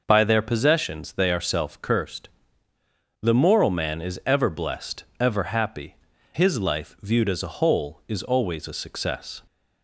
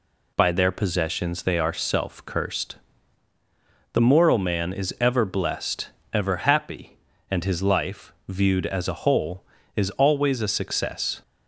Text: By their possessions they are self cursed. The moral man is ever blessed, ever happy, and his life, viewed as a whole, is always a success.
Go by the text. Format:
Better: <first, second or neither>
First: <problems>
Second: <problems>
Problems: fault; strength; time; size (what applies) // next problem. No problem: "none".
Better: second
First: skips "and"; at 6.1 s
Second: none